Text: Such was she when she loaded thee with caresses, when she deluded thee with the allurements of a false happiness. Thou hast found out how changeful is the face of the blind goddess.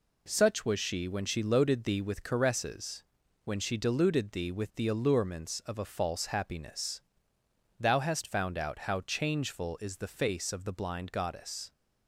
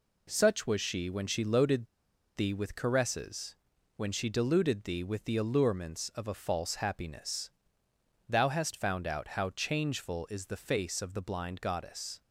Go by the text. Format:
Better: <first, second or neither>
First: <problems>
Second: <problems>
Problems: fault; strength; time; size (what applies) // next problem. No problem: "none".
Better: first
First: none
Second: pauses between "loaded" and "thee"; noticeable; at 1.8 s; 0.51 s long